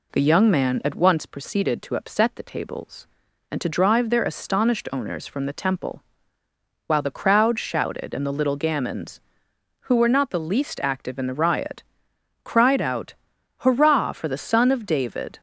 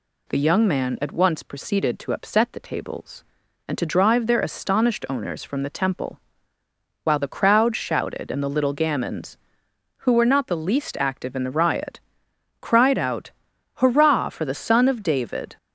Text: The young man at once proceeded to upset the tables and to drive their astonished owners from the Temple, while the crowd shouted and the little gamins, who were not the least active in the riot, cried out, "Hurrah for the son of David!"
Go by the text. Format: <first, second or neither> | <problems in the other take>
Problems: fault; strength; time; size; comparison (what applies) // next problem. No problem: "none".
second | starts louder than the rest; slight; until 1.4 s; 3 dB